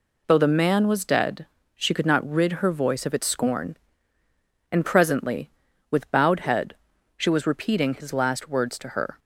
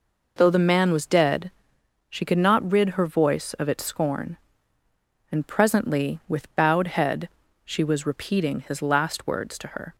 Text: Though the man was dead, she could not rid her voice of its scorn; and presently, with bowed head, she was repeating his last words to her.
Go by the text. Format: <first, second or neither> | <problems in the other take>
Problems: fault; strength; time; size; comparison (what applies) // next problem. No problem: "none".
neither | none